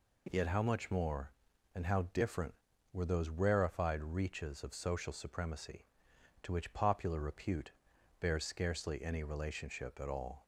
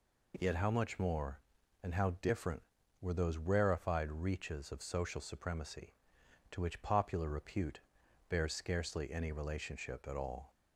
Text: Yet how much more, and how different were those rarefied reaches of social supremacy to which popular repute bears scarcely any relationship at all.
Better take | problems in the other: neither | pauses between "repute" and "bears"; noticeable; the same in both

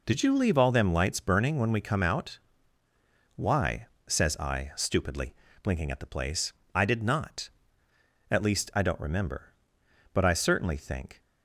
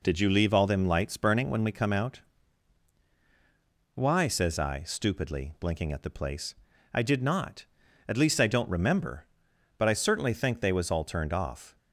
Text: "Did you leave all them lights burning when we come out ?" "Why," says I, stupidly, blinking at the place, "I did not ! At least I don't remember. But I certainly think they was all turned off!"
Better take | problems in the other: second | stops before "they was all turned off"; at 11.2 s

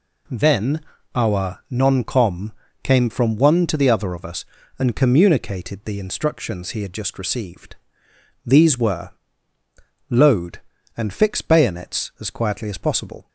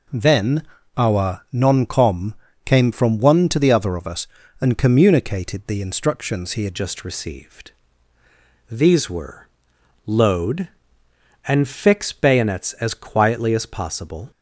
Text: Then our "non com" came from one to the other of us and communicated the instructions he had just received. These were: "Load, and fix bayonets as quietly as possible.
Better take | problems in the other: first | pauses between "Then" and "our"; slight; at 0.6 s; 0.34 s long; slight in the first // pauses between "com" and "came"; slight; at 2.3 s; 0.30 s long; slight in the first // changes voice at "just"; from 6.7 s on; 7.6 s long

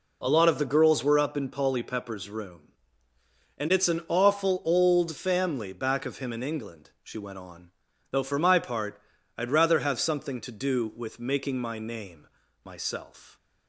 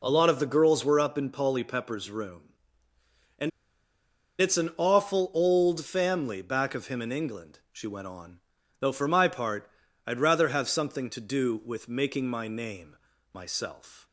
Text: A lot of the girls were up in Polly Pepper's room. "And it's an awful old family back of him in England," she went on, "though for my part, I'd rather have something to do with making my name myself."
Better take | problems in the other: first | pauses between "And" and "it's"; noticeable; at 3.5 s; 0.91 s long // pauses between "name" and "myself"; slight; at 12.9 s; 0.34 s long; slight in the first

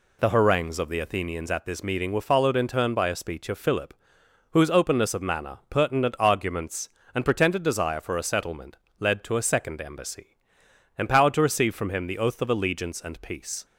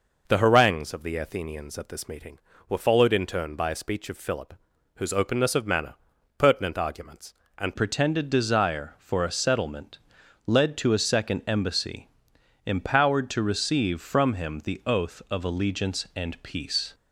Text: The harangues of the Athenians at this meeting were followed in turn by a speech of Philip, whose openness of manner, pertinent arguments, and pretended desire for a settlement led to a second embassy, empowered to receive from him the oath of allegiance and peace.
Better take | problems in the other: first | changes voice at "pretended"; from 7.7 s on; 9.2 s long // pauses between "settlement" and "led"; noticeable; at 9.9 s; 0.50 s long; slight in the first

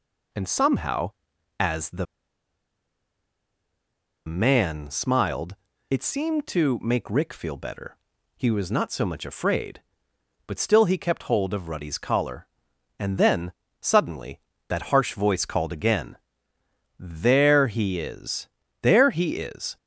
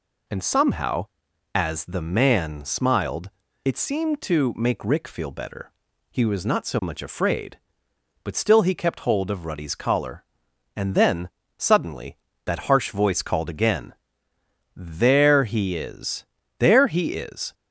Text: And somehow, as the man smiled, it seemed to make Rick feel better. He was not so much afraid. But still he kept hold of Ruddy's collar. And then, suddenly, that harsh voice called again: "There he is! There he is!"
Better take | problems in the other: second | pauses between "the" and "man"; strong; at 2.0 s; 2.2 s long

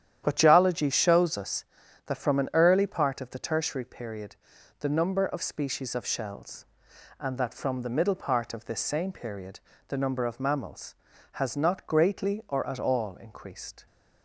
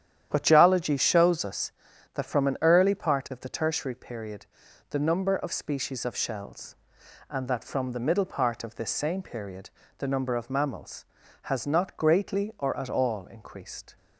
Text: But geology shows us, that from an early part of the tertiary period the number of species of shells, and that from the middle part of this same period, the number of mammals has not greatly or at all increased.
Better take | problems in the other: neither | starts louder than the rest; strong; the same in both // pauses between "period" and "the"; the same in both

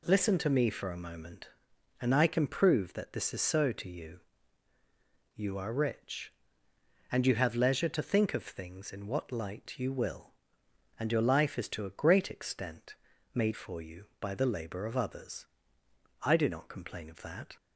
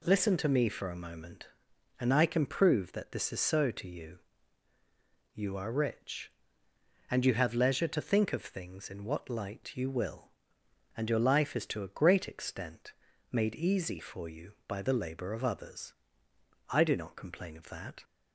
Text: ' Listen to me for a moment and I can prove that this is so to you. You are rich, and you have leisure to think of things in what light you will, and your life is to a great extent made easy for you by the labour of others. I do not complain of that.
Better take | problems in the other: second | pauses between "extent" and "made"; at 12.9 s; 0.38 s long; also in the second // skips "easy"; at 13.5 s

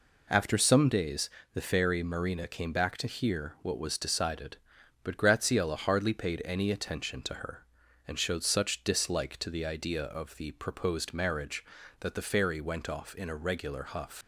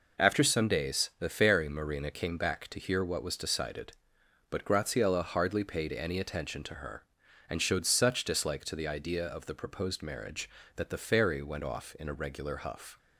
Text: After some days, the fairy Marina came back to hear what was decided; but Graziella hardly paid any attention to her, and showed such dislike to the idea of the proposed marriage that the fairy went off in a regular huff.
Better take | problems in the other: second | leaves "huff" unfinished; at 14.2 s; 110 ms

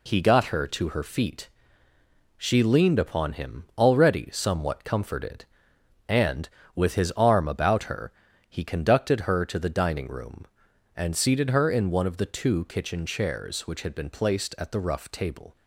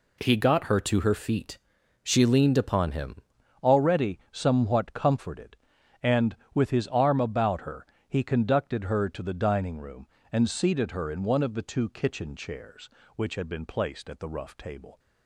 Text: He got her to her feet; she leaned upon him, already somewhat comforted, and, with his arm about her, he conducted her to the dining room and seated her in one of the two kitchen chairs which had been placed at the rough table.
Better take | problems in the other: first | changes voice at "already"; from 3.6 s on; 11.3 s long

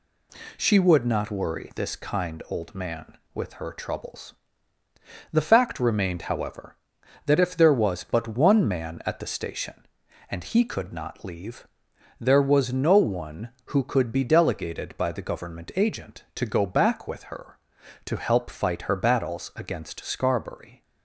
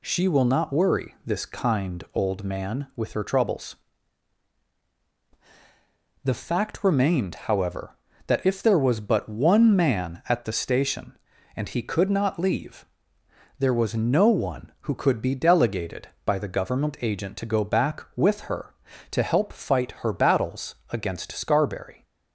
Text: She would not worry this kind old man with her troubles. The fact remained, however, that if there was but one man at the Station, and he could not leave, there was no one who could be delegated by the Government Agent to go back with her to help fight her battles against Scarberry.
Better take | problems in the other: first | says "will" for "would"; at 0.2 s // pauses between "battles" and "against"; slight; at 20.7 s; 0.16 s long

